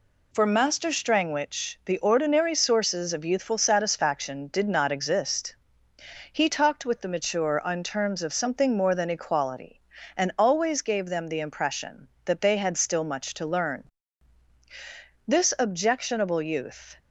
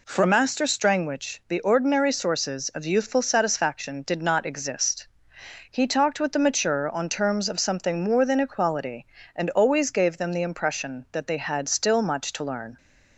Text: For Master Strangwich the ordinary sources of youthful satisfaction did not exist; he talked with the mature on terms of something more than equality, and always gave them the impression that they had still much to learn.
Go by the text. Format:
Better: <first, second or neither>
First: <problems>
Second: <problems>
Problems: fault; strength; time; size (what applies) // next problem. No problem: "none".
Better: second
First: goes on to say "This objectionable youth"; strong; from 15.2 s on; 1.6 s long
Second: none